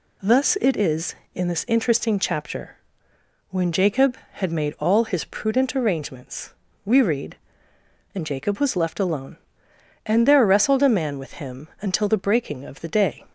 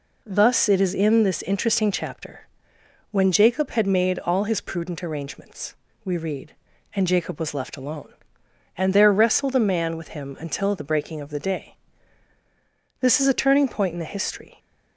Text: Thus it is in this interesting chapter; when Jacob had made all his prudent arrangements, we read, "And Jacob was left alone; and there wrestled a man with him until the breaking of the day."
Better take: first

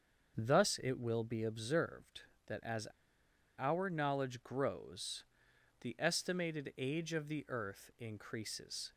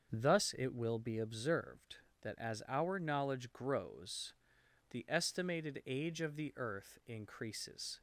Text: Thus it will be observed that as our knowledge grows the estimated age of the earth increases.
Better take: second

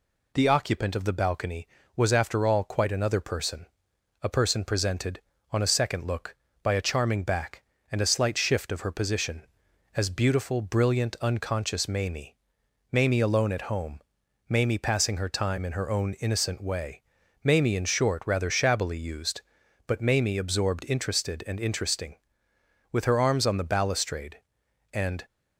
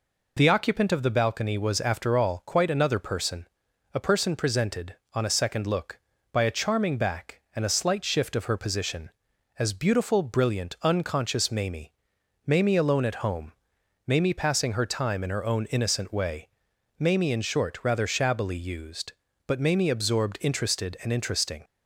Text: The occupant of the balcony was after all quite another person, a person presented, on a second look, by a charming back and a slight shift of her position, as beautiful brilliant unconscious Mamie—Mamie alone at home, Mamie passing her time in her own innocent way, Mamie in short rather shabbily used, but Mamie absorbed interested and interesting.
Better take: second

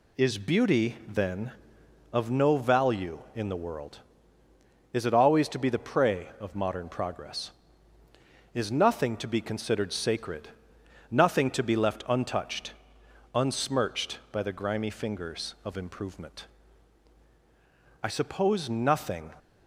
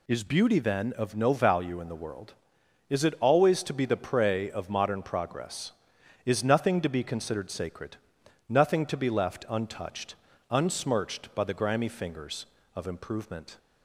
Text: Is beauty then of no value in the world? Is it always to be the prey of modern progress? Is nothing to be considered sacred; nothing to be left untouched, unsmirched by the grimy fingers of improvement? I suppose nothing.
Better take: first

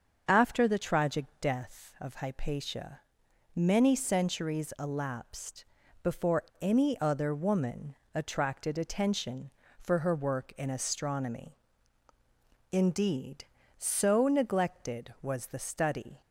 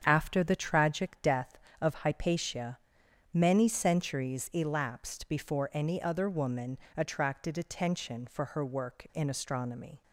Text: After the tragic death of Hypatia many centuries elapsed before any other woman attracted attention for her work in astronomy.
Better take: second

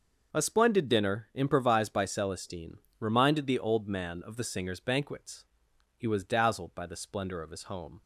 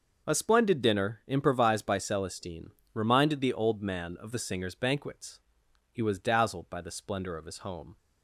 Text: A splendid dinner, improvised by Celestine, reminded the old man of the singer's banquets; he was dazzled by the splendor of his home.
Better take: neither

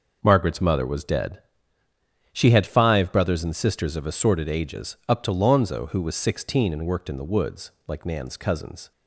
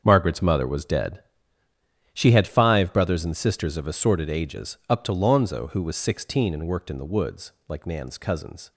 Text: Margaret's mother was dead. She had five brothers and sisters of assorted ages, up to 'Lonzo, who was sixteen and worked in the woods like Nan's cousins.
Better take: first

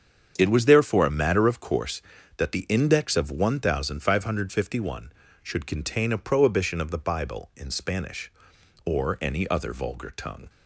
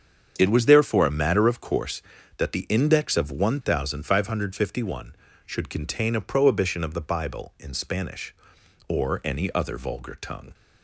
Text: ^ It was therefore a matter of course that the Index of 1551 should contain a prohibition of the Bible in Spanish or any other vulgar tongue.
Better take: neither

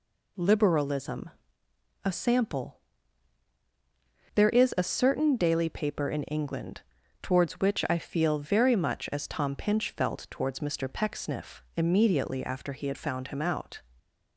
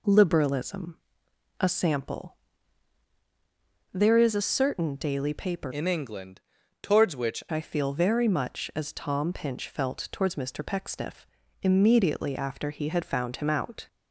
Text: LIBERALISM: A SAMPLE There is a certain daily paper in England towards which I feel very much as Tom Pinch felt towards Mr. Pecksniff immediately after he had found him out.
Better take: first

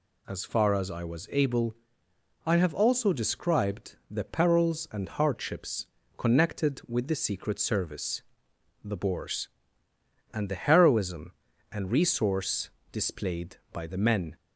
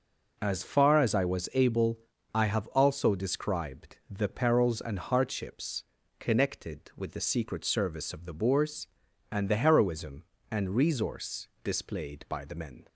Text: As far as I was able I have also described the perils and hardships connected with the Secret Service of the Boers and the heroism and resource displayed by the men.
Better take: second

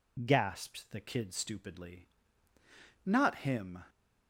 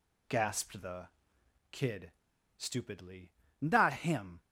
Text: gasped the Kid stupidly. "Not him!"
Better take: first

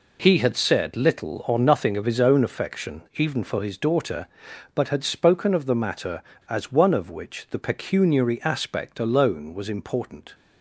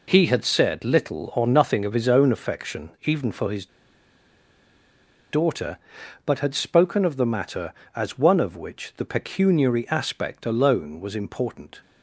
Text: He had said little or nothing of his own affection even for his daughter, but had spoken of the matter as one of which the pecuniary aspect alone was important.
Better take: first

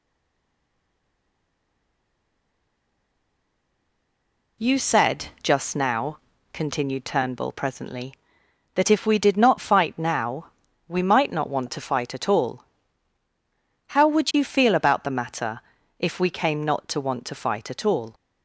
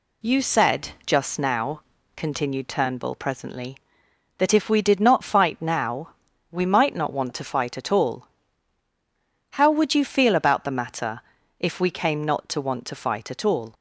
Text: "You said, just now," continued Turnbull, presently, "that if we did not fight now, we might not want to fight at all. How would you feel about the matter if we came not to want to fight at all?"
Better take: second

